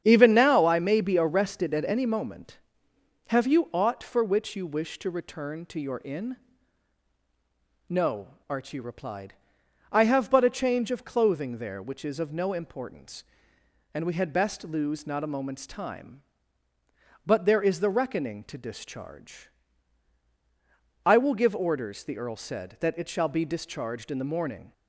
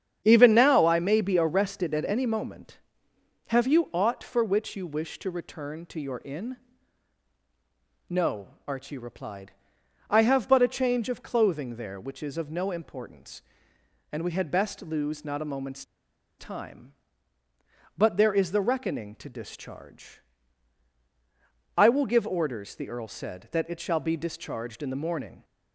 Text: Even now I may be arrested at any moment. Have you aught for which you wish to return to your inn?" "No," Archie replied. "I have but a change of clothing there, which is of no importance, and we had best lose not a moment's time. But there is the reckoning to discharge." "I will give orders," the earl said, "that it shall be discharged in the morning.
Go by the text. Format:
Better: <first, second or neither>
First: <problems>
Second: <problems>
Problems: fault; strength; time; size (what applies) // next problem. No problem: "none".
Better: first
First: starts louder than the rest; strong; until 1.0 s; 8 dB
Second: starts louder than the rest; strong; until 1.2 s; 8 dB // pauses between "moment's" and "time"; noticeable; at 15.8 s; 0.56 s long